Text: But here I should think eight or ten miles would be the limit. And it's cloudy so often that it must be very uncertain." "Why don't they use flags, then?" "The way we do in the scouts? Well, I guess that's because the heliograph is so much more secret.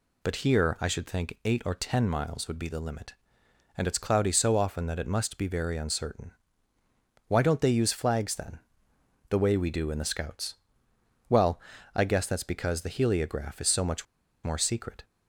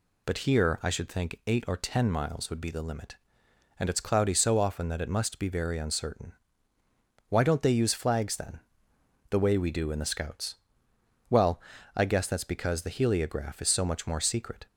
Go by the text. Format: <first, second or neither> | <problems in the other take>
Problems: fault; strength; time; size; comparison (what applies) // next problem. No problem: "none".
second | pauses between "much" and "more"; at 14.0 s; 0.38 s long